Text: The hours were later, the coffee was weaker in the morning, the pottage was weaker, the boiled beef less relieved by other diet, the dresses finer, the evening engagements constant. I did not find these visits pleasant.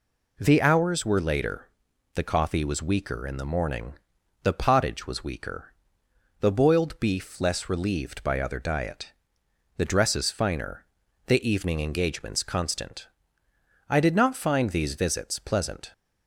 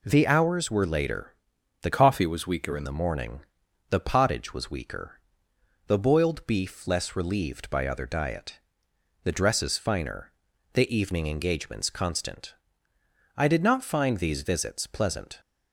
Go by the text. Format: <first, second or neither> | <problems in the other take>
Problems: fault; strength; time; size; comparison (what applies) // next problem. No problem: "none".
first | changes voice from "coffee" to "in"; from 1.9 to 2.8 s; 0.9 s long